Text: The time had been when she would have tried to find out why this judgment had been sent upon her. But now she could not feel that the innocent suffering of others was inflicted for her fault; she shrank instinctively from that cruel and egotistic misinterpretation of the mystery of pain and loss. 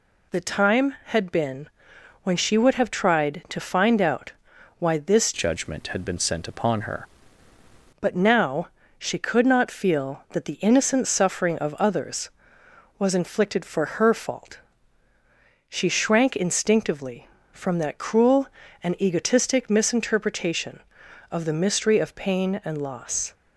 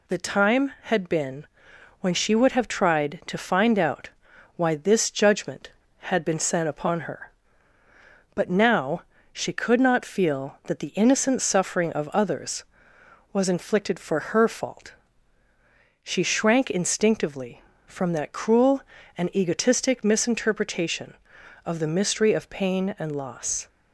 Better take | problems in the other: second | pauses between "been" and "when"; noticeable; at 1.6 s; 0.54 s long; noticeable in the second // pauses between "out" and "why"; at 4.3 s; 0.44 s long; also in the second // changes voice from "judgment" to "her"; from 5.3 to 7.0 s; 1.7 s long // pauses between "now" and "she"; slight; at 8.6 s; 0.28 s long; slight in the second // pauses between "for" and "her"; slight; at 13.8 s; 0.16 s long; slight in the second

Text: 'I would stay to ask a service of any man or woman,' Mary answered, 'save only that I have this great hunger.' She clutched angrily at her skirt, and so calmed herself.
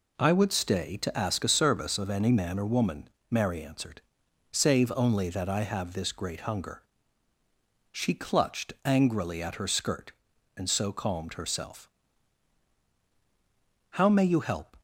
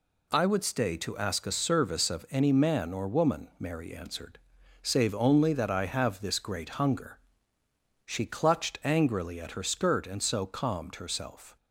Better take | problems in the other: second | goes on to say "How may you help"; noticeable; from 13.9 s on; 0.84 s long

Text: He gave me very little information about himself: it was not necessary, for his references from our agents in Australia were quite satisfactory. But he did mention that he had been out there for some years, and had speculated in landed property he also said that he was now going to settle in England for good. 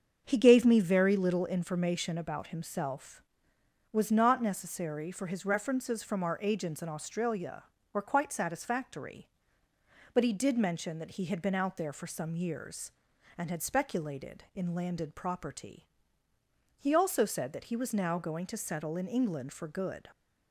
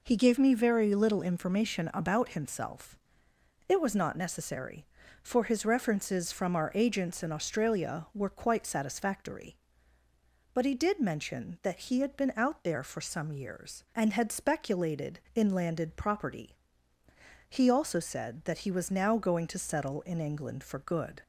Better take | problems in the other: second | starts louder than the rest; strong; until 1.2 s; 7 dB // skips "it"; at 3.5 s // pauses between "property" and "he"; noticeable; at 15.8 s; 0.92 s long; noticeable in the second

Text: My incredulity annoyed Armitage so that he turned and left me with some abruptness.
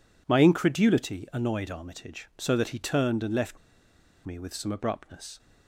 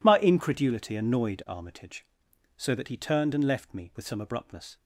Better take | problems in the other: second | pauses between "left" and "me"; noticeable; at 3.5 s; 0.68 s long

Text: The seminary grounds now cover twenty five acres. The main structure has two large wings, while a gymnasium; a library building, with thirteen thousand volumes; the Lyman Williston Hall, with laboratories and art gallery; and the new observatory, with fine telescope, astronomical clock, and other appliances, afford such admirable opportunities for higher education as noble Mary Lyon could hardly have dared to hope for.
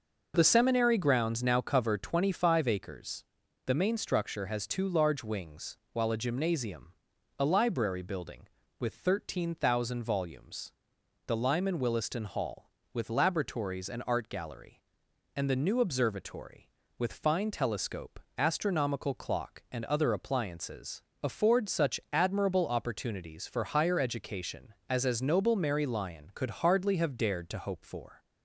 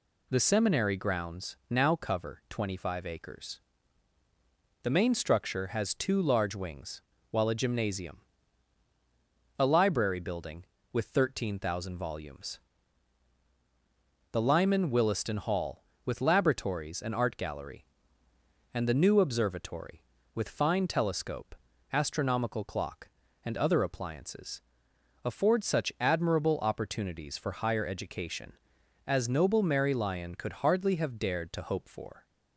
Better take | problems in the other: second | says "as" twice; at 25.0 s

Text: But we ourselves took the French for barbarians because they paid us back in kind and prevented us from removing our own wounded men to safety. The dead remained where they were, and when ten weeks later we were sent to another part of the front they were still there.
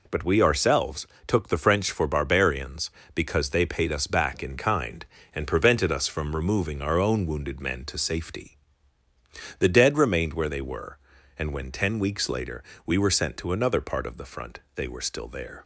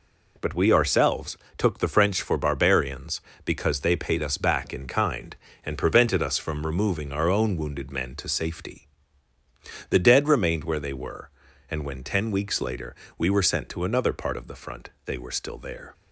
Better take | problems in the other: neither | pauses between "ourselves" and "took"; slight; the same in both // pauses between "later" and "we"; slight; the same in both // pauses between "front" and "they"; slight; the same in both

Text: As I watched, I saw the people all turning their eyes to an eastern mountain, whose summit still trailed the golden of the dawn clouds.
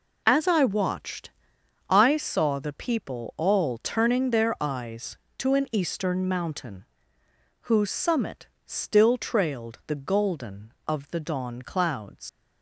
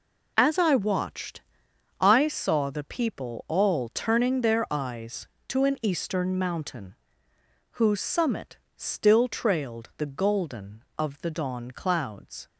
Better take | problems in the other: second | pauses between "summit" and "still"; slight; at 8.4 s; 0.21 s long; slight in the second // leaves "clouds" unfinished; at 12.2 s; 85 ms

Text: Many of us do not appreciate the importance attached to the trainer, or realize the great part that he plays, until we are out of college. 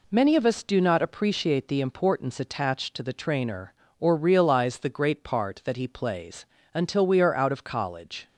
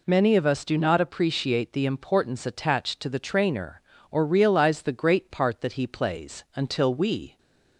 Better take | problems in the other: first | stops before "are out of college"; at 7.3 s

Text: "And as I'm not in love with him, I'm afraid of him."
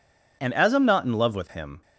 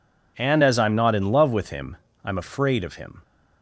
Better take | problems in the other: second | stops before "I'm afraid of him"; at 1.8 s

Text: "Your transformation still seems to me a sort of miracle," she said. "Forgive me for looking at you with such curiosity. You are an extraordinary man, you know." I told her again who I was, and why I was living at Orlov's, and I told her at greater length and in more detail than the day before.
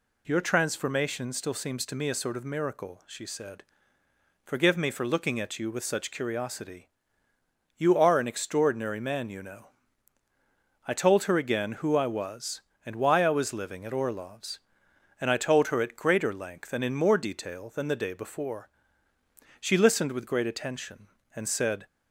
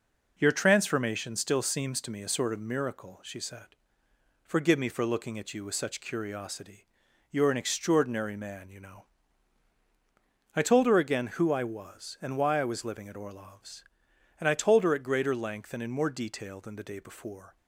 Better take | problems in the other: second | goes on to say "She listened with great attention and said"; strong; from 19.5 s on; 2.2 s long

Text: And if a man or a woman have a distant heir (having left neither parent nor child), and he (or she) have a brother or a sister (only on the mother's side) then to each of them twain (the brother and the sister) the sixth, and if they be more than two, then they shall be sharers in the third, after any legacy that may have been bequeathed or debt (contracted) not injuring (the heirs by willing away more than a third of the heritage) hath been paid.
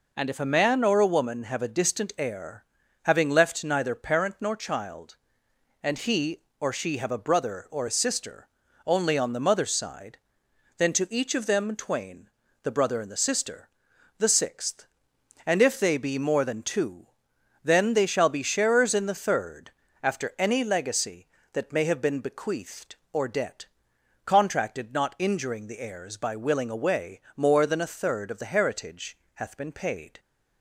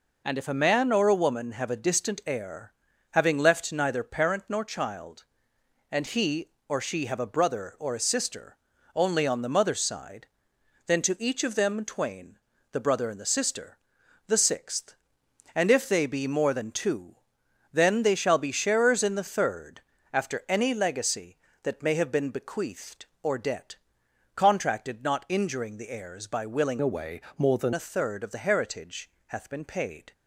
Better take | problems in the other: first | changes voice from "away" to "than"; from 26.8 to 27.7 s; 0.9 s long // pauses between "away" and "more"; slight; at 27.2 s; 0.16 s long; slight in the first

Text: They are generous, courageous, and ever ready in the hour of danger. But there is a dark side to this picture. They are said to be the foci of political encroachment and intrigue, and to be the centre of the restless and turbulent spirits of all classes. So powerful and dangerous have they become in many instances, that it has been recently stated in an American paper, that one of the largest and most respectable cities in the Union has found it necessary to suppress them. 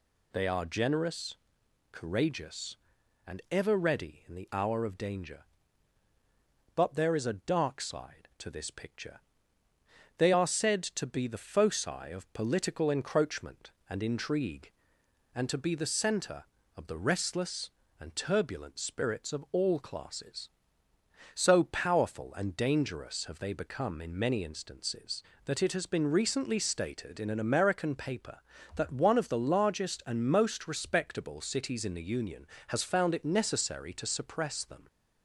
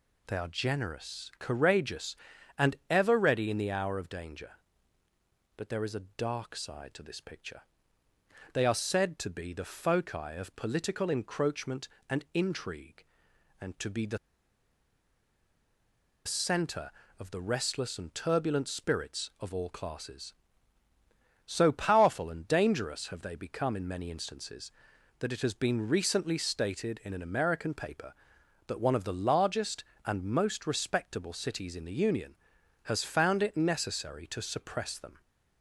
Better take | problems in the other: first | pauses between "the" and "centre"; strong; at 14.1 s; 2.0 s long

